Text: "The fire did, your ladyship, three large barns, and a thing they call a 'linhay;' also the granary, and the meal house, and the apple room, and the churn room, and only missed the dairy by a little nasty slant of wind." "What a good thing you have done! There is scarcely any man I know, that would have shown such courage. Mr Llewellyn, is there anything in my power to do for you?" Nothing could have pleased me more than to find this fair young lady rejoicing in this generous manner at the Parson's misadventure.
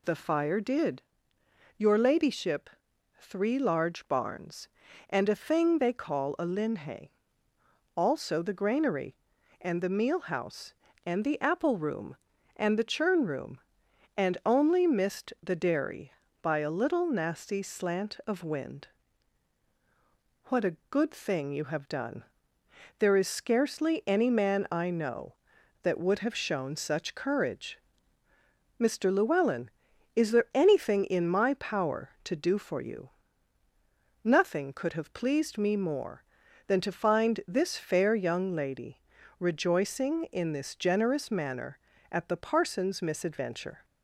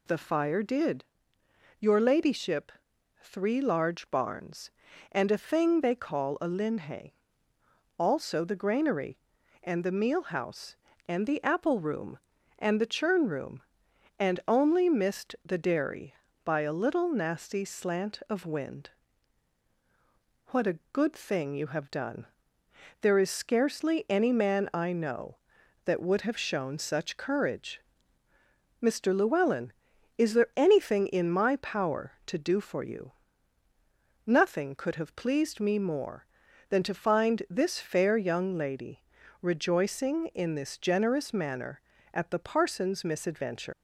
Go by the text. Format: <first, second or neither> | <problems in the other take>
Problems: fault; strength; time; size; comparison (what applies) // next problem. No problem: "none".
first | pauses between "lady" and "rejoicing"; at 39.0 s; 0.40 s long; also in the first // leaves "misadventure" unfinished; at 43.7 s; 140 ms